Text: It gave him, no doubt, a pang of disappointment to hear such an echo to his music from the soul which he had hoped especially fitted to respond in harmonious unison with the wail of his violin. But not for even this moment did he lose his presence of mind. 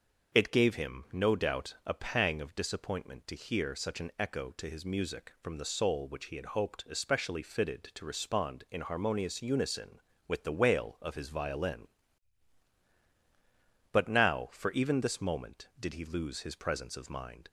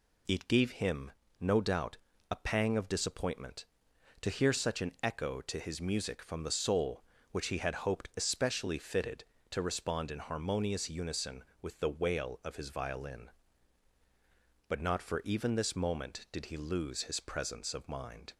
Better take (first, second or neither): second